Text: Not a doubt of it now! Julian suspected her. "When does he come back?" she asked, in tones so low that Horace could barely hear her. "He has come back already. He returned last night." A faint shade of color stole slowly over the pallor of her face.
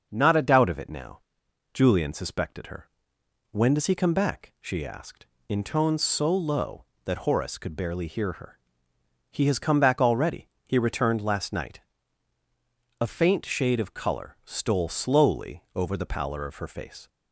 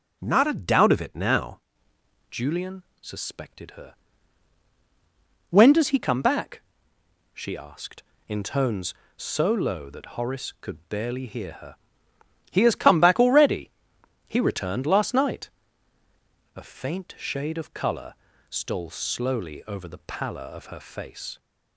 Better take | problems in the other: first | starts louder than the rest; until 1.2 s; 6.5 dB; also in the first // changes voice at "Julian"; from 2.3 s on; 19.0 s long // pauses between "Julian" and "suspected"; slight; at 2.8 s; 0.18 s long // pauses between "color" and "stole"; at 18.1 s; 0.38 s long

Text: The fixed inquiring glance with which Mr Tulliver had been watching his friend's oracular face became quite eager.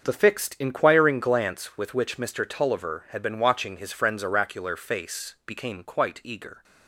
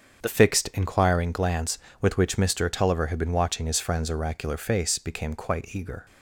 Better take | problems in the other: first | starts louder than the rest; strong; until 1.2 s; 7 dB; also in the first // changes voice at "fixed"; from 0.2 s on; 5.8 s long

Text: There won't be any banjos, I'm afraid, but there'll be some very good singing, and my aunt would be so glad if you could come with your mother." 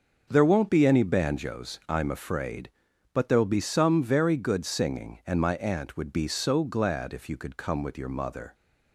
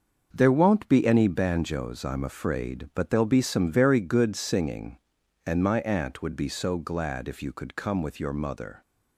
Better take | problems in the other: neither | starts louder than the rest; the same in both

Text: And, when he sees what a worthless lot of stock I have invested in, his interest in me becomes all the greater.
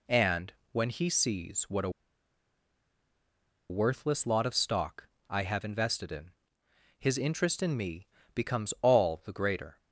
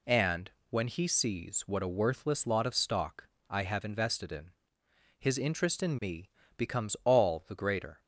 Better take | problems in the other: second | pauses between "a" and "worthless"; strong; at 1.8 s; 1.8 s long // pauses between "stock" and "I"; slight; at 5.0 s; 0.22 s long; slight in the second // pauses between "me" and "becomes"; slight; at 8.0 s; 0.28 s long; slight in the second

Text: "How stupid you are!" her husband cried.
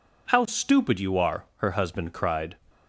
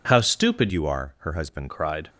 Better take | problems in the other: first | changes voice from "you" to "husband"; from 0.7 to 1.6 s; 0.9 s long

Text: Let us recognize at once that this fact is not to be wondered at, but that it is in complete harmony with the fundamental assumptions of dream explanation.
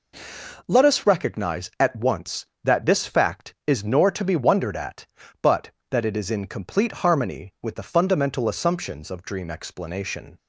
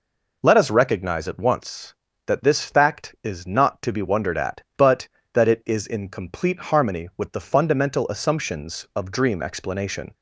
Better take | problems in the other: second | says "nor" for "not"; at 3.8 s

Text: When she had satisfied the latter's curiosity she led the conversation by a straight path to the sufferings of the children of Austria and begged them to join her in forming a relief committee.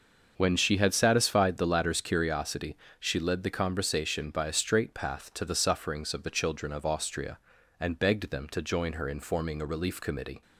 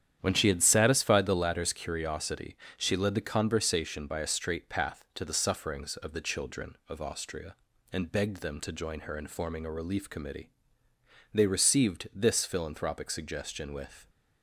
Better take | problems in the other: first | starts louder than the rest; strong; until 1.2 s; 9.5 dB // pauses between "curiosity" and "she"; slight; at 2.5 s; 0.18 s long; slight in the first // goes on to say "They received this philanthropic suggestion with"; strong; from 11.3 s on; 2.7 s long

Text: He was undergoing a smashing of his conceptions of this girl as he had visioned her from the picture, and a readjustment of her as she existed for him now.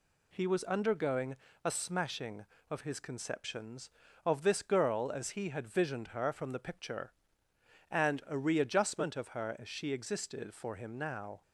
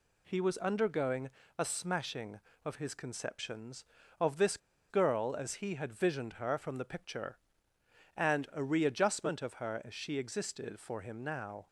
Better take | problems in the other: first | pauses between "undergoing" and "a"; slight; at 1.2 s; 0.26 s long; slight in the first // pauses between "this" and "girl"; slight; at 4.5 s; 0.32 s long

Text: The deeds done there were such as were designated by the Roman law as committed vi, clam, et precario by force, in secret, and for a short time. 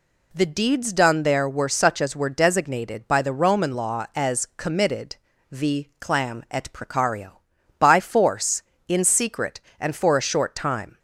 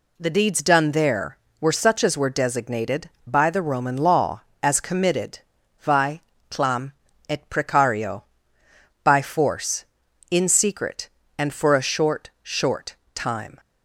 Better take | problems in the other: first | pauses between "committed" and "vi"; at 5.3 s; 0.42 s long; slight in the first // says "short" twice; at 12.4 s

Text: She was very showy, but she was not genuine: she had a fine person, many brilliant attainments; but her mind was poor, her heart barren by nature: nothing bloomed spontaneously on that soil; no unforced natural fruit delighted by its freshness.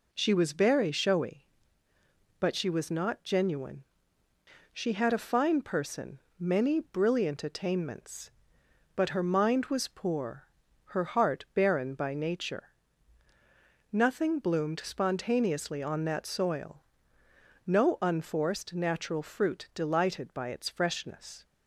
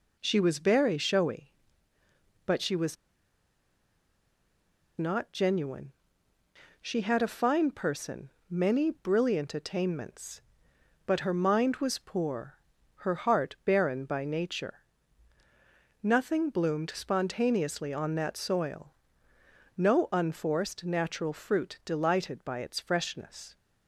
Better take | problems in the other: first | pauses between "was" and "not"; strong; at 2.9 s; 2.0 s long

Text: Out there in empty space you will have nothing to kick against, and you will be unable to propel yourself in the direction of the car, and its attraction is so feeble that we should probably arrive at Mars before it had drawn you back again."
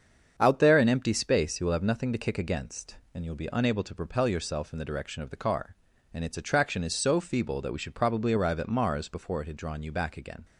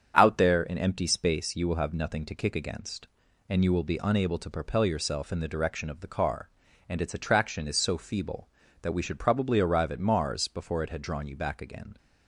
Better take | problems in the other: neither | starts louder than the rest; strong; the same in both

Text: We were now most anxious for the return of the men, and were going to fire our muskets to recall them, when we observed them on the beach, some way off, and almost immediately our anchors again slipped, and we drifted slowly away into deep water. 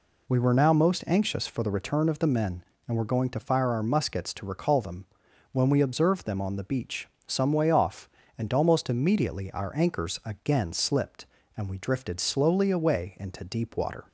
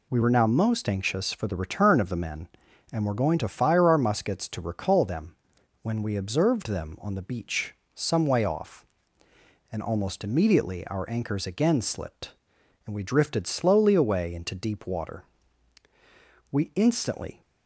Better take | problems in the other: first | goes on to say "We instantly"; noticeable; from 16.5 s on; 0.90 s long

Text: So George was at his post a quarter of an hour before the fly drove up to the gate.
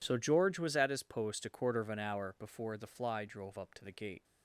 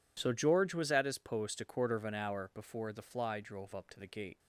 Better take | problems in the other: neither | none

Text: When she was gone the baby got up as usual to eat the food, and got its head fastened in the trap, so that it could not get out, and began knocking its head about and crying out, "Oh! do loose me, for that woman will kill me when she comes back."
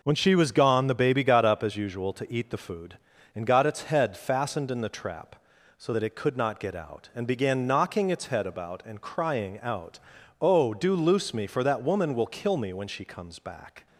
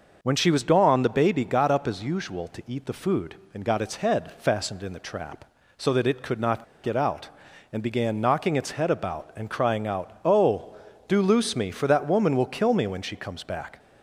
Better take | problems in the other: first | pauses between "not" and "get"; slight; at 6.6 s; 0.19 s long

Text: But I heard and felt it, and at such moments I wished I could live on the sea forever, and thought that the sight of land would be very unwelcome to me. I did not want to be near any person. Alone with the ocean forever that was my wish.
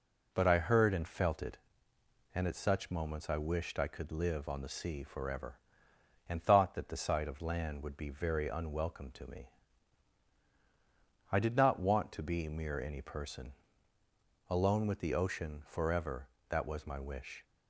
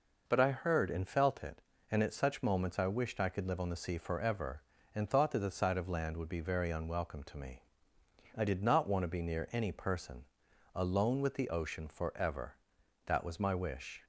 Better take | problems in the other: second | says "mere" for "near"; at 12.4 s

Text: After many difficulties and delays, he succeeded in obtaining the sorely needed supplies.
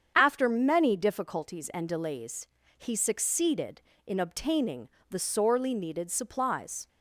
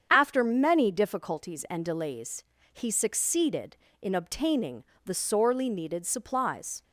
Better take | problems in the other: neither | starts louder than the rest; strong; the same in both // pauses between "obtaining" and "the"; slight; the same in both

